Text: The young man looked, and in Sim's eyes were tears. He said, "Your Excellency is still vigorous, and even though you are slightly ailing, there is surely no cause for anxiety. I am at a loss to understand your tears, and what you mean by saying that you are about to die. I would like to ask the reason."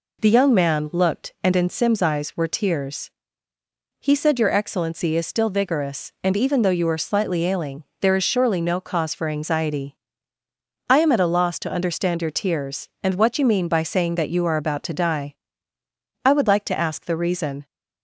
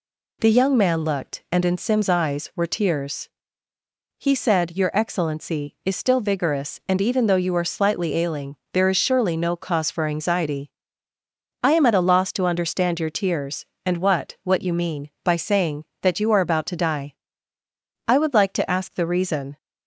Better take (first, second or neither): first